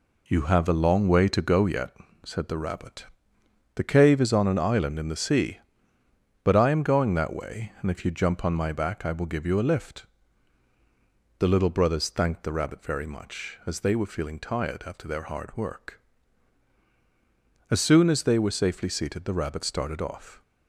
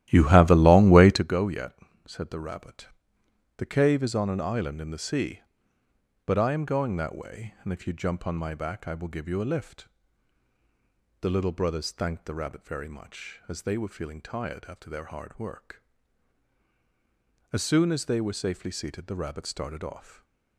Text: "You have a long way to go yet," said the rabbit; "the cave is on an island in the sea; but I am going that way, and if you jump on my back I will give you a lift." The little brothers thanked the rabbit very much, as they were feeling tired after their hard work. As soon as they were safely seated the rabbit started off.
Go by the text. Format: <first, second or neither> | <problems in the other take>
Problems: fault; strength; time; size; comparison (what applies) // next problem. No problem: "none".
first | starts louder than the rest; strong; until 1.3 s; 14 dB